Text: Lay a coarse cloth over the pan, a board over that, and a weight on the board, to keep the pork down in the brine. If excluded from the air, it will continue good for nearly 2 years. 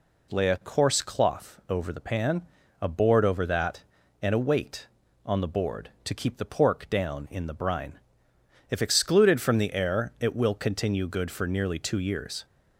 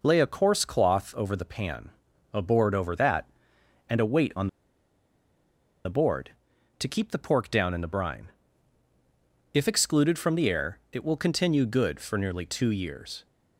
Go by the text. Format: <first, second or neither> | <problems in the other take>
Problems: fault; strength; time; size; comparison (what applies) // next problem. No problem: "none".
first | pauses between "on" and "the"; strong; at 4.4 s; 1.3 s long